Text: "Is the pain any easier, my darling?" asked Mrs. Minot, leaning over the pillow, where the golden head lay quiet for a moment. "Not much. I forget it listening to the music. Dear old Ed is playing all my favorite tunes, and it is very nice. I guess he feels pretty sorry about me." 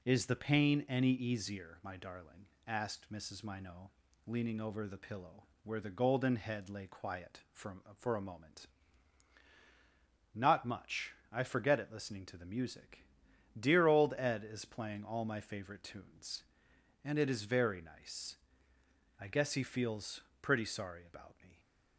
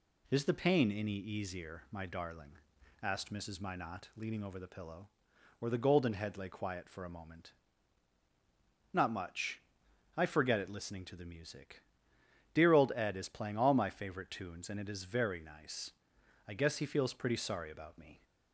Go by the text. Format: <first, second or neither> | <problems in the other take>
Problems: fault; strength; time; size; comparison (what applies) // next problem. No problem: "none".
second | says "for" twice; at 7.9 s // pauses between "feels" and "pretty"; slight; at 20.2 s; 0.20 s long